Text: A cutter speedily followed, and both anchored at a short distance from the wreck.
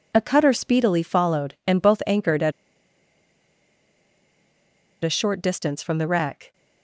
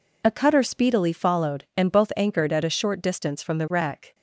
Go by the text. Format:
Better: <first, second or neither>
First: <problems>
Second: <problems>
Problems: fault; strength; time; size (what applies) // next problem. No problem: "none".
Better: second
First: pauses between "at" and "a"; strong; at 2.5 s; 2.5 s long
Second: none